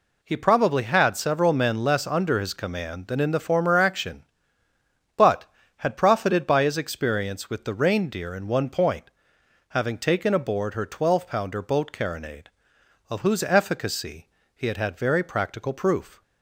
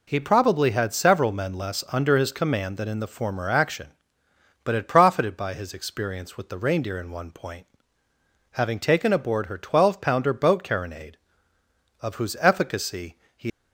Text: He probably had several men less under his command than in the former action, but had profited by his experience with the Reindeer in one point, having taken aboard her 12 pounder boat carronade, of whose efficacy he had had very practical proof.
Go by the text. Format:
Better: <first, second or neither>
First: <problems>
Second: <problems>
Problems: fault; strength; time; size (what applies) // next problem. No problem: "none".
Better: first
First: pauses between "efficacy" and "he"; slight; at 14.2 s; 0.26 s long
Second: pauses between "efficacy" and "he"; slight; at 13.1 s; 0.18 s long // stops before "had had very practical proof"; at 13.5 s